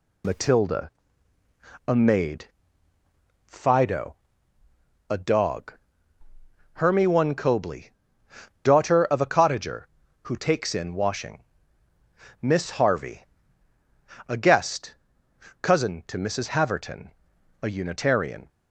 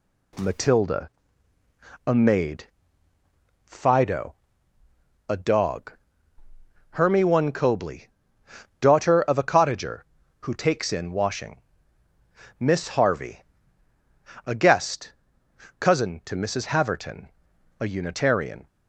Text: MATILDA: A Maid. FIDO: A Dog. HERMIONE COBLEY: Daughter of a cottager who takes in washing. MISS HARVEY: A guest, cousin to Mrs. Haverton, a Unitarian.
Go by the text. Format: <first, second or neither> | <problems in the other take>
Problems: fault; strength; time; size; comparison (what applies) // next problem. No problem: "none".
second | loses the start of "MATILDA"; at 0.2 s; 105 ms